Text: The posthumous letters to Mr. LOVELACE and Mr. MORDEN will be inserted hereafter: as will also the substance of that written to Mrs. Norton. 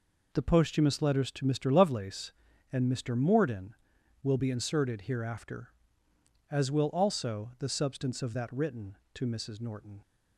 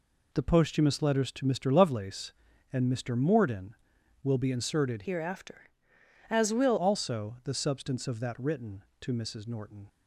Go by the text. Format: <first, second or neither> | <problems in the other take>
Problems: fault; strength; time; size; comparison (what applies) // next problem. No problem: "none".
first | changes voice from "hereafter" to "will"; from 5.0 to 6.7 s; 1.7 s long